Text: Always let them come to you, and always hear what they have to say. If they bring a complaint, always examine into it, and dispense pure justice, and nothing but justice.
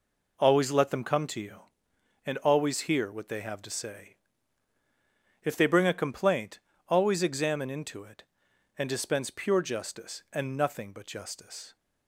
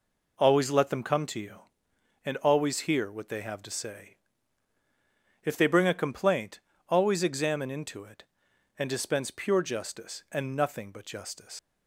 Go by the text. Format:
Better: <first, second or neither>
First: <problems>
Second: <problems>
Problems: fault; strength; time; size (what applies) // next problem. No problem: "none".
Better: first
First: none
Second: leaves "justice" unfinished; at 11.5 s; 155 ms